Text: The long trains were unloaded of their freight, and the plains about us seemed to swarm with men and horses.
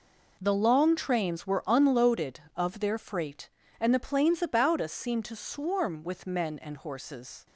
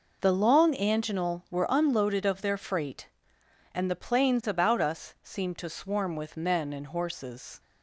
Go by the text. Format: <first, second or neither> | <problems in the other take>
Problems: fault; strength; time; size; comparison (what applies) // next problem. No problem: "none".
first | says "anginal" for "trains"; at 0.7 s